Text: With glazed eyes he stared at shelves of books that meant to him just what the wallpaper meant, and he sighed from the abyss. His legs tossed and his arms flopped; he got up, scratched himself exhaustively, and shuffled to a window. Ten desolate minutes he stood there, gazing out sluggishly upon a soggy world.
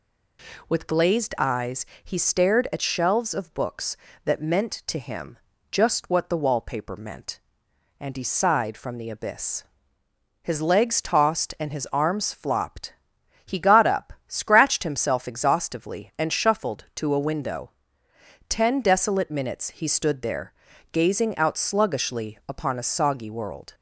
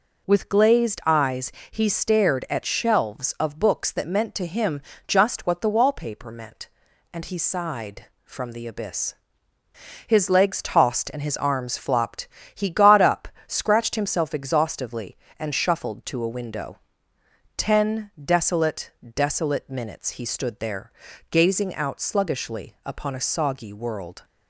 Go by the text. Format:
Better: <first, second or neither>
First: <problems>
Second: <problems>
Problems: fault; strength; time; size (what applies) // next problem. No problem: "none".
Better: first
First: pauses between "eyes" and "he"; slight; at 1.8 s; 0.20 s long // pauses between "him" and "just"; slight; at 5.3 s; 0.32 s long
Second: pauses between "eyes" and "he"; slight; at 1.5 s; 0.18 s long // pauses between "him" and "just"; slight; at 4.8 s; 0.26 s long // says "desolate" twice; at 19.1 s